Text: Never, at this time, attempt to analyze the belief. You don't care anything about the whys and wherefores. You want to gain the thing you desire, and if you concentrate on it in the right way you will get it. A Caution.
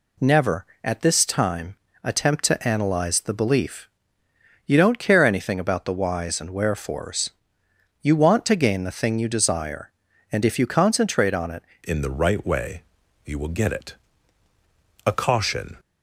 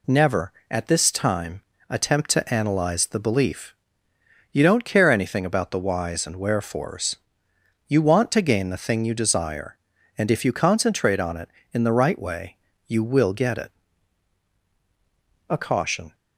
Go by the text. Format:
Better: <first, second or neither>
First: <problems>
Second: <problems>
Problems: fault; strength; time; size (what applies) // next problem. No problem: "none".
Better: second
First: changes voice at "in"; from 11.8 s on; 3.9 s long // pauses between "way" and "you"; at 12.8 s; 0.42 s long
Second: pauses between "way" and "you"; slight; at 12.5 s; 0.30 s long